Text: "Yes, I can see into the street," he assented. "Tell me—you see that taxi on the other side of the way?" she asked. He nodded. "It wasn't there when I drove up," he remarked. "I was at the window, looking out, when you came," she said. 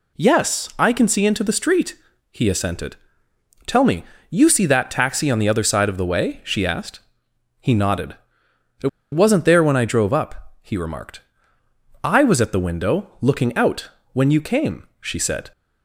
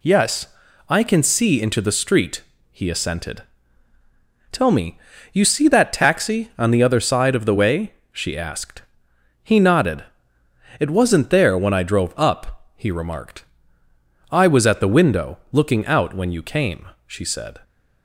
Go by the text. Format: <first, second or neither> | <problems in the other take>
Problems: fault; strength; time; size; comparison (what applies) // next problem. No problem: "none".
second | pauses between "It" and "wasn't"; slight; at 8.8 s; 0.23 s long